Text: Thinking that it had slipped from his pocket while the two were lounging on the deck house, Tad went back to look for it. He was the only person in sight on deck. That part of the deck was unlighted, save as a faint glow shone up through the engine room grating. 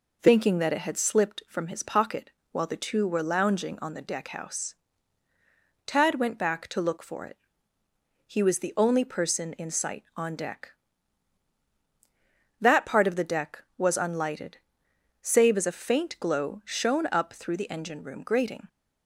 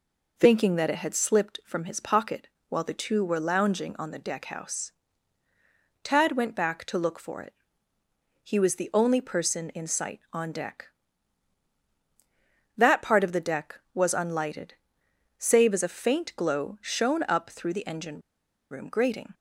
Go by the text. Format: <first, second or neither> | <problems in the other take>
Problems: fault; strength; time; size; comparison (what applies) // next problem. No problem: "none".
first | pauses between "pocket" and "while"; slight; at 2.4 s; 0.20 s long; slight in the first // pauses between "engine" and "room"; noticeable; at 18.2 s; 0.50 s long